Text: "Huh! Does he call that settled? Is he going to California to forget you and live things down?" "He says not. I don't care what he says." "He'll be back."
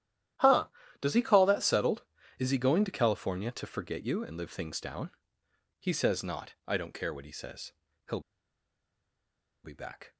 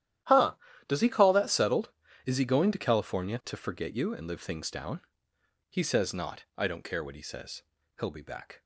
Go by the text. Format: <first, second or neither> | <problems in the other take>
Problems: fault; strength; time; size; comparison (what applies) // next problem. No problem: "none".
second | starts louder than the rest; strong; until 1.7 s; 12 dB; strong in the second // pauses between "He'll" and "be"; strong; at 8.1 s; 1.4 s long